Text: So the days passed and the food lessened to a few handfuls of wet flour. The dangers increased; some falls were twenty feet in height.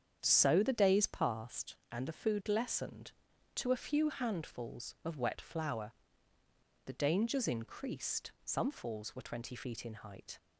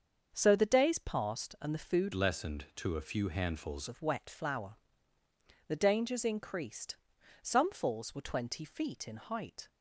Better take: first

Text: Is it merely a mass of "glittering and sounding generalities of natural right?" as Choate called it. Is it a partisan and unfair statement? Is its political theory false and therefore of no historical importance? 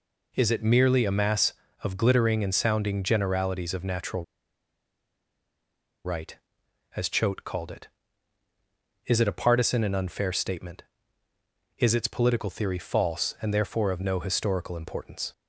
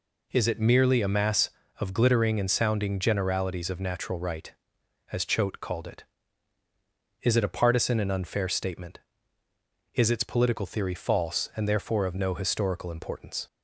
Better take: second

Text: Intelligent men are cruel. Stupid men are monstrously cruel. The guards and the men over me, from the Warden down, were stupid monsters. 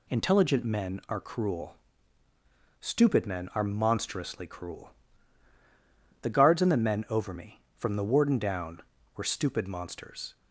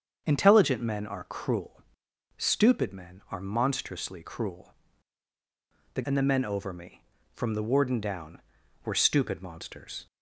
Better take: first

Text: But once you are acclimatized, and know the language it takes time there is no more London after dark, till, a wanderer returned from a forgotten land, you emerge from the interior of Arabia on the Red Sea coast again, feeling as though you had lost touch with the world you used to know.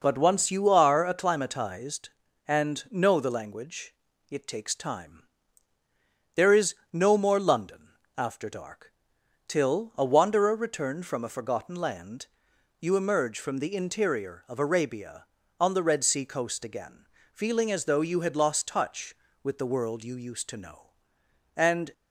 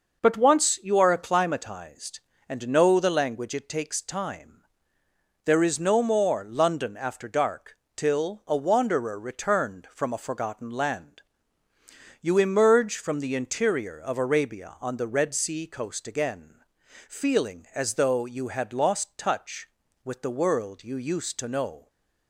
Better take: second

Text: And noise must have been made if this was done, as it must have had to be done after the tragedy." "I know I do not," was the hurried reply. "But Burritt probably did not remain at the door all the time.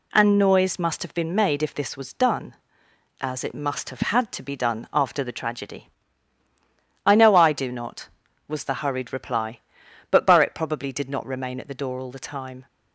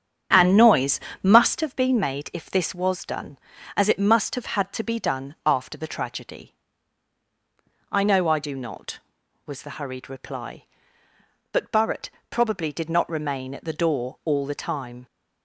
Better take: first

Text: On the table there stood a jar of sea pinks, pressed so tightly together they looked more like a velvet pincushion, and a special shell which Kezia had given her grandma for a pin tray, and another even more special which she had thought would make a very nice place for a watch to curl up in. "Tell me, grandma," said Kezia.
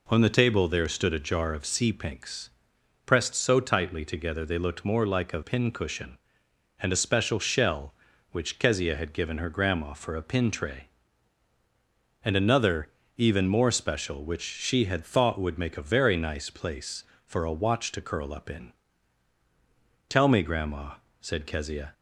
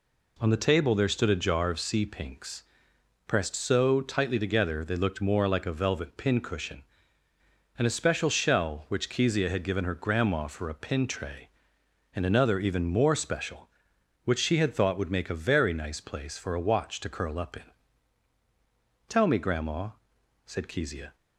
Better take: second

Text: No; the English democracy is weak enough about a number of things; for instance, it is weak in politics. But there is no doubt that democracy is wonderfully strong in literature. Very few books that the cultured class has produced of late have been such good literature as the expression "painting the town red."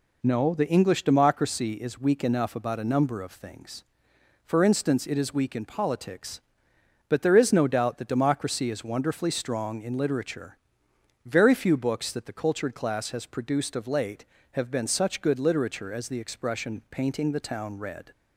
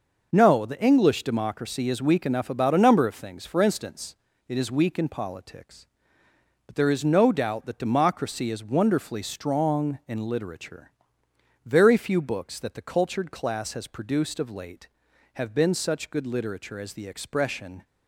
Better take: first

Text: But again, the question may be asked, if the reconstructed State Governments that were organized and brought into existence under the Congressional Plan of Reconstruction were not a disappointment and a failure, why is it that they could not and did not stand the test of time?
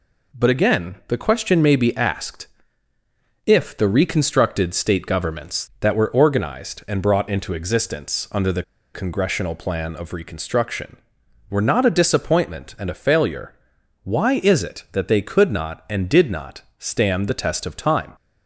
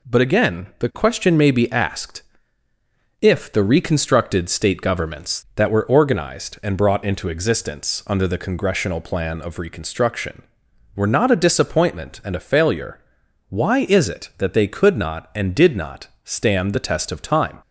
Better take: second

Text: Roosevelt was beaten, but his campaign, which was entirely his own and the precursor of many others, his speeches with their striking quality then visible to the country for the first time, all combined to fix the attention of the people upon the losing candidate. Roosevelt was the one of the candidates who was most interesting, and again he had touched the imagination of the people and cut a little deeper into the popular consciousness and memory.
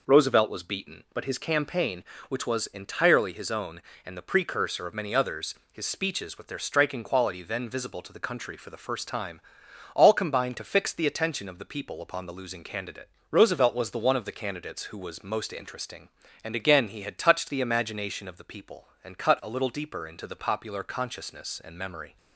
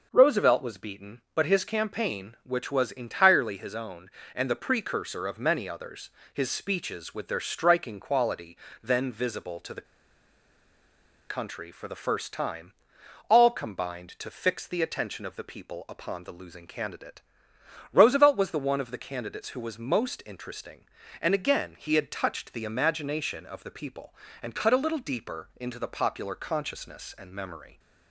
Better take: first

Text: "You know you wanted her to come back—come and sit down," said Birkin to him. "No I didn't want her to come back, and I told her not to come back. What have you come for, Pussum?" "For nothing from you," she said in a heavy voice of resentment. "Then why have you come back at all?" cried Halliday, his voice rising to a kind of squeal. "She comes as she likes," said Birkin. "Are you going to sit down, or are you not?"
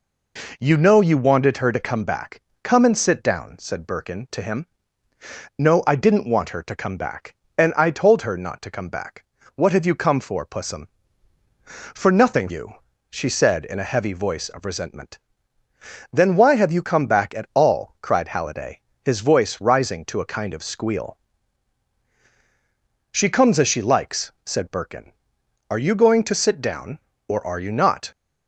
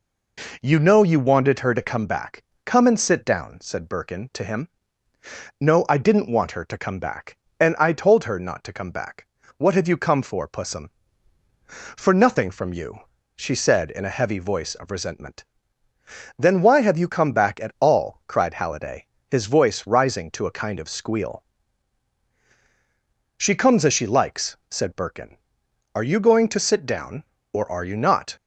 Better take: second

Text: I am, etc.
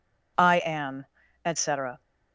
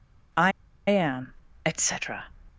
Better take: first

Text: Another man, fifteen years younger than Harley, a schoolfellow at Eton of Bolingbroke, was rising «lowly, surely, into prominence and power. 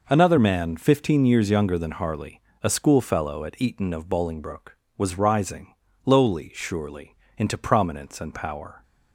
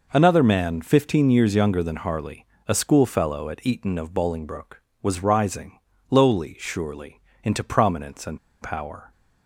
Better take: first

